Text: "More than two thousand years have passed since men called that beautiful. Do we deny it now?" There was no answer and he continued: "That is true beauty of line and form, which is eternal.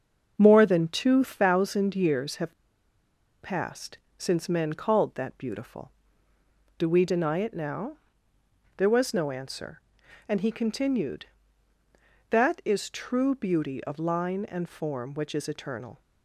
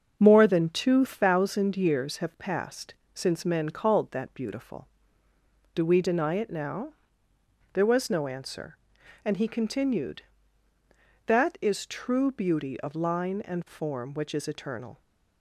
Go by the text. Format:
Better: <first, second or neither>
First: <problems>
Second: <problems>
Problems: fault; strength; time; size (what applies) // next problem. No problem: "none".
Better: second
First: starts louder than the rest; until 1.3 s; 6.5 dB // pauses between "have" and "passed"; noticeable; at 2.5 s; 0.86 s long // pauses between "passed" and "since"; slight; at 3.9 s; 0.18 s long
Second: starts louder than the rest; until 1.2 s; 6.5 dB // pauses between "passed" and "since"; slight; at 2.9 s; 0.18 s long